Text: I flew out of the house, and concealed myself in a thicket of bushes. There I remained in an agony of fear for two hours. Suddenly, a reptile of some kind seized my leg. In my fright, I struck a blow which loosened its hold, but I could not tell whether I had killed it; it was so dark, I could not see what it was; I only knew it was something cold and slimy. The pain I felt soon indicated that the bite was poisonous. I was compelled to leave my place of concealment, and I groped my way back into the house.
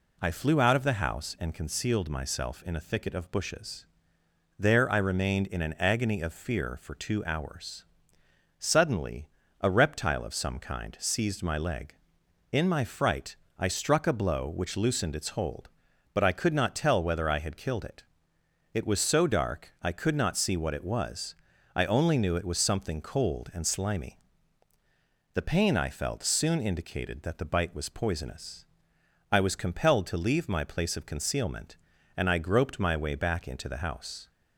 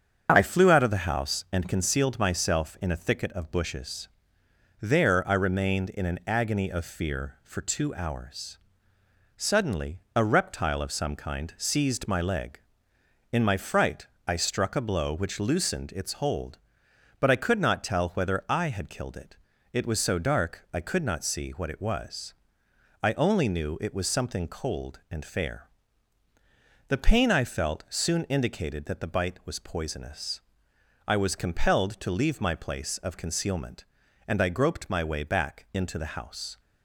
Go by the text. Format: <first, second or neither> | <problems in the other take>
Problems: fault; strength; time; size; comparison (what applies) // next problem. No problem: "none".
first | starts louder than the rest; strong; until 1.3 s; 7 dB // says "fair" for "slimy"; at 25.2 s